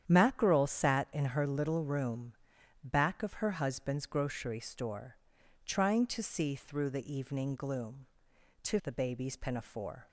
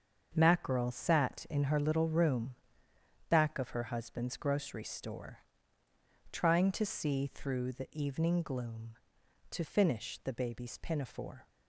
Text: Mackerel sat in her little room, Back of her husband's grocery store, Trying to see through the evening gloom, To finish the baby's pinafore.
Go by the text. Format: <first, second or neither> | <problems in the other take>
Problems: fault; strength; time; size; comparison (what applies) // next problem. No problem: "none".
second | starts louder than the rest; strong; until 1.0 s; 9.5 dB; also in the second // skips "finish"; at 8.7 s